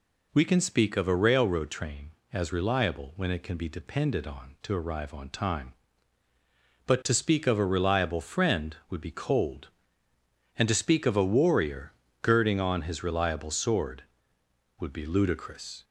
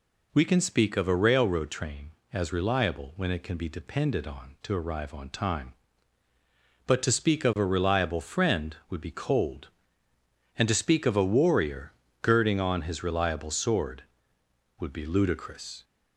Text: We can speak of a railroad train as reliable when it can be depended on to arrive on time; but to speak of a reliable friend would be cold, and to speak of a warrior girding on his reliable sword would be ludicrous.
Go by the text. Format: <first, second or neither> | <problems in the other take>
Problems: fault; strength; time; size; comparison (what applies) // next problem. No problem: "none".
neither | pauses between "warrior" and "girding"; slight; the same in both